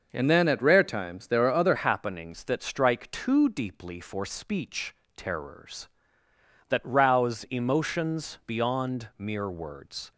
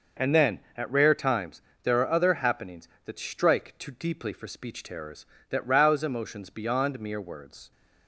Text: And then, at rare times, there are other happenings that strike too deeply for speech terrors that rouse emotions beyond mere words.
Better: second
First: starts louder than the rest; noticeable; until 1.1 s; 6 dB // changes voice at "happenings"; from 1.7 s on; 8.4 s long // pauses between "speech" and "terrors"; slight; at 4.9 s; 0.22 s long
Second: none

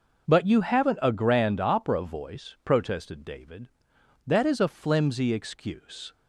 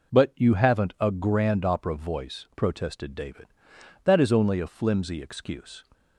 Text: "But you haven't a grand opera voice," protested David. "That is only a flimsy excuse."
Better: second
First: skips "only"; at 4.5 s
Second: none

